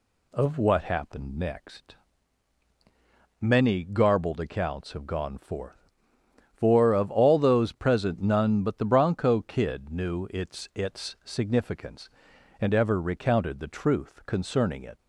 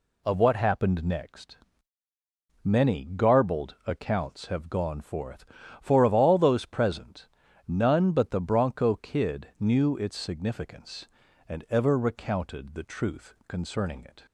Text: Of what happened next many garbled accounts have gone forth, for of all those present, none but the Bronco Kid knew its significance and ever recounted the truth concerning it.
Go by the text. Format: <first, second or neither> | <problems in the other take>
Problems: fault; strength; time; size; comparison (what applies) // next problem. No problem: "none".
second | pauses between "next" and "many"; strong; at 1.9 s; 1.4 s long; also in the second // says "its" twice; at 10.7 s